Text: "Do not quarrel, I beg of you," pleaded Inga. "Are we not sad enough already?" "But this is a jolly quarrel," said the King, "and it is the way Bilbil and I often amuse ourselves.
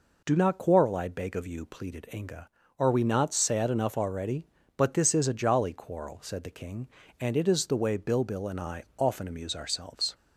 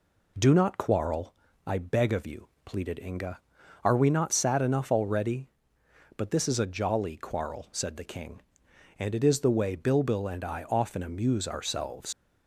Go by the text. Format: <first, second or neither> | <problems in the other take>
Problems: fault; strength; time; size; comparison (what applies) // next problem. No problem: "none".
first | leaves "ourselves" unfinished; at 12.1 s; 105 ms